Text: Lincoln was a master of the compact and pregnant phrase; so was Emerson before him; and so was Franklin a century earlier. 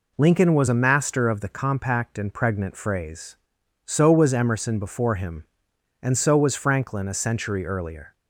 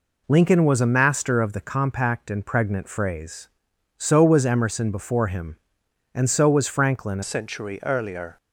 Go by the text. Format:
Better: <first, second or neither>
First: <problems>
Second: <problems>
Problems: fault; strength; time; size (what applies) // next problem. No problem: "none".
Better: first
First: none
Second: changes voice at "century"; from 7.2 s on; 1.1 s long